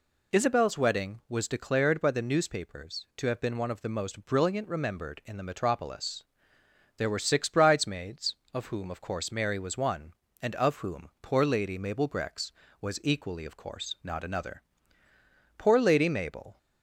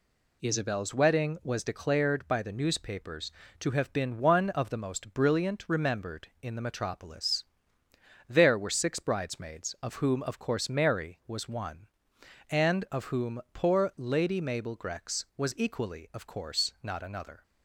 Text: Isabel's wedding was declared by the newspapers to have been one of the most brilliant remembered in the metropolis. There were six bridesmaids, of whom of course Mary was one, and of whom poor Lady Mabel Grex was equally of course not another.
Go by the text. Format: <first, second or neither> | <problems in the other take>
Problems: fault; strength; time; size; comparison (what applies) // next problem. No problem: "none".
second | goes on to say "Poor Lady Mabel"; noticeable; from 15.5 s on; 1.0 s long